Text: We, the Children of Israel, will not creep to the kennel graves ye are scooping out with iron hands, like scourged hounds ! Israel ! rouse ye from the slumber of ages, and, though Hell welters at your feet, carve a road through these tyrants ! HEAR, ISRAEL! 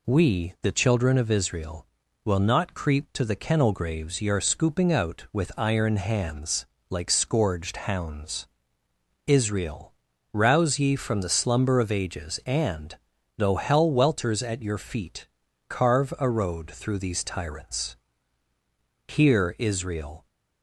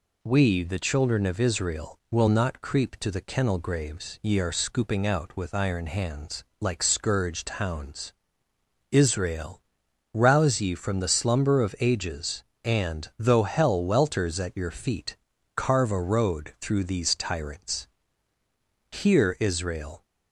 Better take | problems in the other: neither | none

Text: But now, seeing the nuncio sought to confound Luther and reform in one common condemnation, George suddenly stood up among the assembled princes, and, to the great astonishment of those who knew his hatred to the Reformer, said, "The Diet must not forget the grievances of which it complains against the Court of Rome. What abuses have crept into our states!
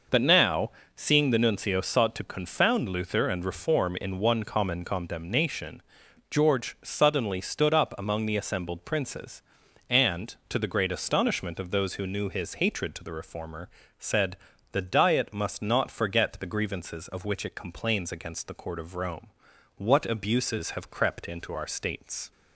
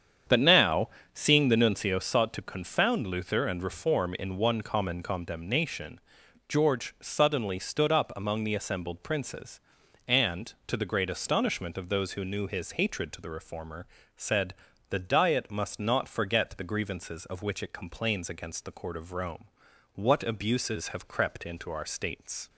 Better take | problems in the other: first | starts louder than the rest; strong; until 2.0 s; 8 dB

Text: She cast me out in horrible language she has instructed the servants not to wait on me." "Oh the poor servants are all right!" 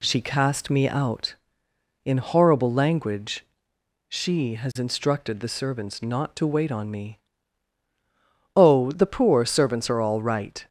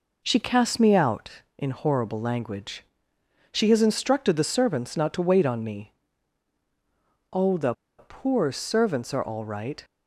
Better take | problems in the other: first | pauses between "language" and "she"; noticeable; at 2.8 s; 0.68 s long; noticeable in the first // pauses between "the" and "poor"; slight; at 7.7 s; 0.24 s long

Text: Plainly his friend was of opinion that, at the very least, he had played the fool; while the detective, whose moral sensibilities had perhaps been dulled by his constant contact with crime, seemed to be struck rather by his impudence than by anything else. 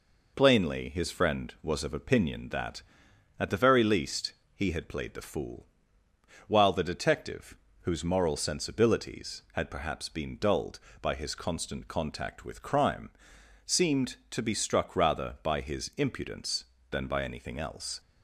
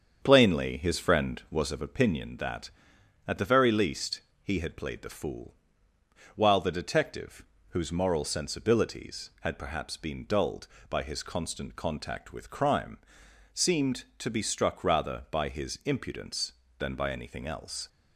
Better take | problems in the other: first | starts louder than the rest; strong; until 1.7 s; 7.5 dB

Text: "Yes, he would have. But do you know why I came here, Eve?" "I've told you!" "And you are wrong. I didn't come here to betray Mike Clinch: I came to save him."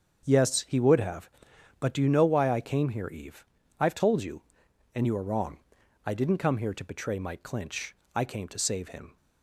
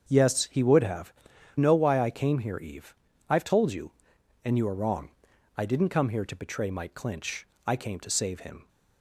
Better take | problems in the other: first | starts louder than the rest; until 1.0 s; 7 dB; also in the first // skips "But do you"; at 1.3 s

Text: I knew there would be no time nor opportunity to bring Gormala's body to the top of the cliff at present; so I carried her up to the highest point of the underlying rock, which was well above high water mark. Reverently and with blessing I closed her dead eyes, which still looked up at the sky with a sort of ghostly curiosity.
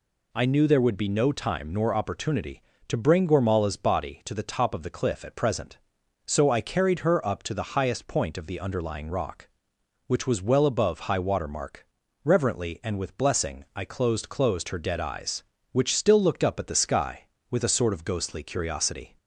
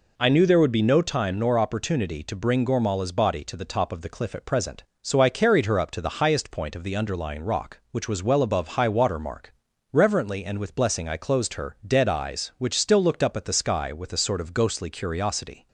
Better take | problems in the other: second | says "closed" twice; at 14.2 s

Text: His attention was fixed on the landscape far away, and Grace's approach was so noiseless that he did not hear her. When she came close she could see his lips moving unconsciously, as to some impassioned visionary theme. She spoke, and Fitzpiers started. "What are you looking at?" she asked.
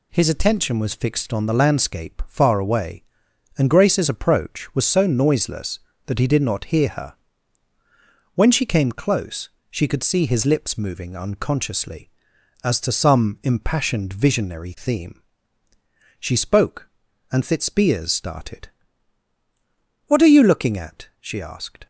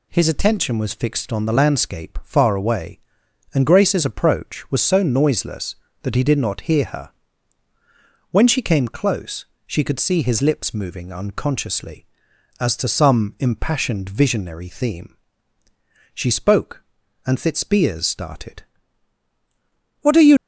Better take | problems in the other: first | pauses between "close" and "she"; slight; at 9.4 s; 0.24 s long; slight in the first // stops before "looking at she asked"; at 20.3 s

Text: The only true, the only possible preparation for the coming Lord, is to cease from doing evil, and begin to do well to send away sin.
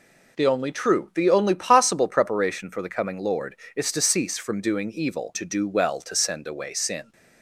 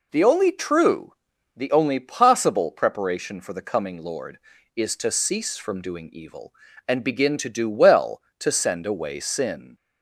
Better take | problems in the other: second | skips "and begin"; at 5.3 s

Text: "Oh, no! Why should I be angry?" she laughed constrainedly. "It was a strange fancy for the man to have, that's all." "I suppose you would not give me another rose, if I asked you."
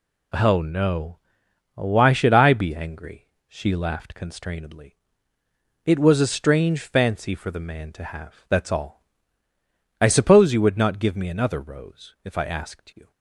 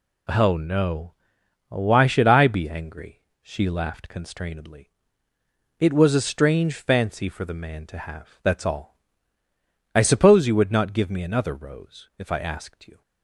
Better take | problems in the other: neither | none

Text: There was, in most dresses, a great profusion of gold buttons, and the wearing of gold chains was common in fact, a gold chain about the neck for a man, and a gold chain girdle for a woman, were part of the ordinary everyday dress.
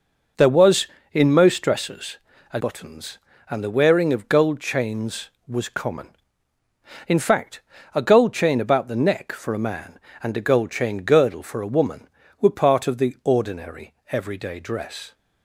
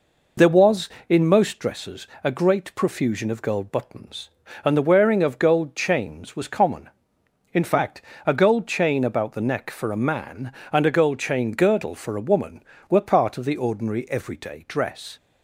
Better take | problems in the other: second | skips "great profusion of gold"; at 2.6 s // pauses between "ordinary" and "everyday"; slight; at 13.9 s; 0.16 s long

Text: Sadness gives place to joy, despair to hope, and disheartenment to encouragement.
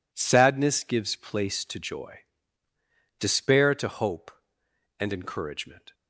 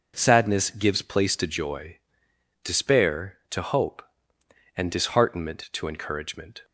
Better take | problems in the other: second | skips "disheartenment to"; at 5.1 s

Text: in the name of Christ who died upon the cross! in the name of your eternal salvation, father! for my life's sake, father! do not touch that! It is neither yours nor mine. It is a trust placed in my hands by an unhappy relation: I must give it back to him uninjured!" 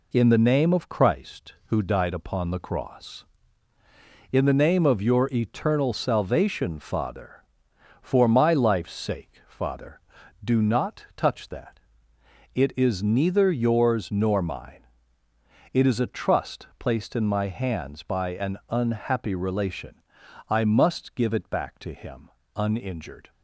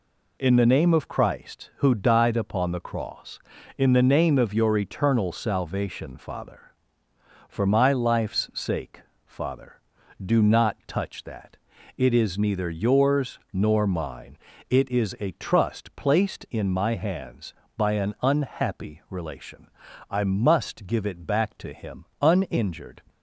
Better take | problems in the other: neither | pauses between "him" and "uninjured"; slight; the same in both

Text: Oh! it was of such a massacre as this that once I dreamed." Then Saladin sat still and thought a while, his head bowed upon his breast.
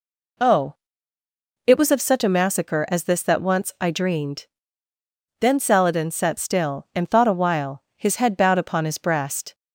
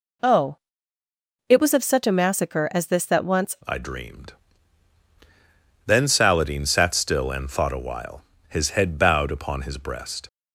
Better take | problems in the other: first | changes voice at "I"; from 3.6 s on; 6.6 s long

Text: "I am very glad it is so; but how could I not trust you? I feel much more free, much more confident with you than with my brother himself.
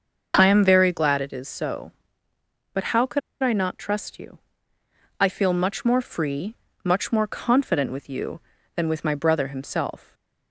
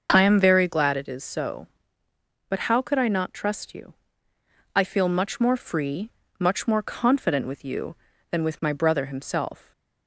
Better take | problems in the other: second | starts louder than the rest; until 1.3 s; 6.5 dB; also in the second // pauses between "could" and "I"; slight; at 3.2 s; 0.23 s long

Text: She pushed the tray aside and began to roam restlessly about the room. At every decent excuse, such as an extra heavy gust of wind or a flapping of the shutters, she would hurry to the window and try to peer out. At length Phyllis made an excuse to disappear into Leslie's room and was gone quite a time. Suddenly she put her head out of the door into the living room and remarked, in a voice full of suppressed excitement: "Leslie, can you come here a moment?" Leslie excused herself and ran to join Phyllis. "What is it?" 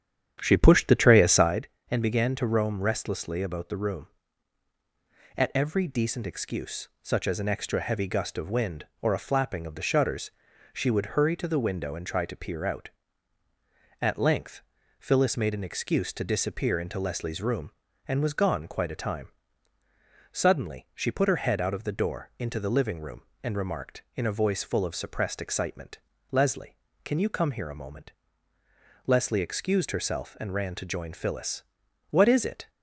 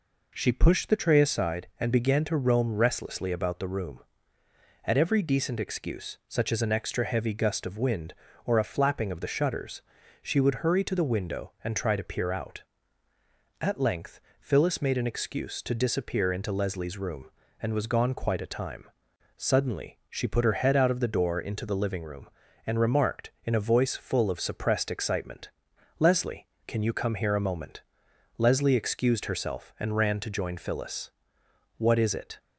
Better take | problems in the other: second | starts louder than the rest; strong; until 1.6 s; 9.5 dB // pauses between "length" and "Phyllis"; at 14.6 s; 0.38 s long; slight in the second

